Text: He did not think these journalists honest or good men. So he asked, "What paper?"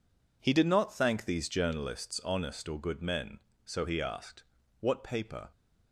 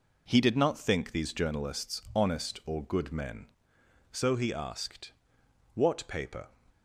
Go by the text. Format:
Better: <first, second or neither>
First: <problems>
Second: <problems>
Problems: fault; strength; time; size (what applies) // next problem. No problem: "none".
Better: second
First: says "thank" for "think"; at 0.9 s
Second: none